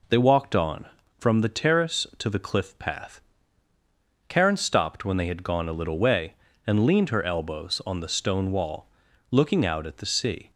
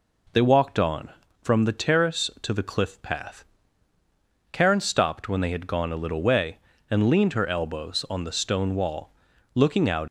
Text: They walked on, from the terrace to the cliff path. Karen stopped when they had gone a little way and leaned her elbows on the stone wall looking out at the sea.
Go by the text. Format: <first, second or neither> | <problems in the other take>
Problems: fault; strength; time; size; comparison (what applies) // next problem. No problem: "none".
first | pauses between "wall" and "looking"; at 9.0 s; 0.44 s long; also in the first // stops before "at the sea"; at 10.0 s